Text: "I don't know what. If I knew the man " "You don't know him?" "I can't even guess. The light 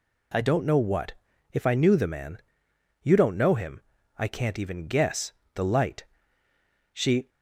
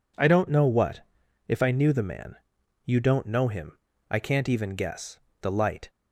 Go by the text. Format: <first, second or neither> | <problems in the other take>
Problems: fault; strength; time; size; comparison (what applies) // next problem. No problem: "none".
second | goes on to say "She"; slight; from 6.9 s on; 0.34 s long